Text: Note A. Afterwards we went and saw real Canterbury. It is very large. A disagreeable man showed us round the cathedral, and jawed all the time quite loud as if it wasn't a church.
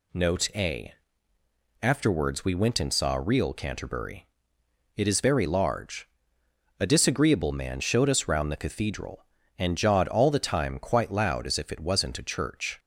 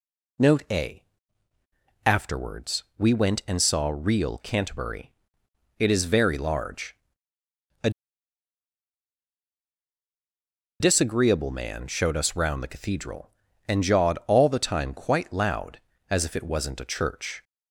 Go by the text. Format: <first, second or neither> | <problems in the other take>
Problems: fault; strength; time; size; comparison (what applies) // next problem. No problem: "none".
first | pauses between "Afterwards" and "we"; slight; at 2.8 s; 0.16 s long // pauses between "A" and "disagreeable"; strong; at 7.8 s; 2.9 s long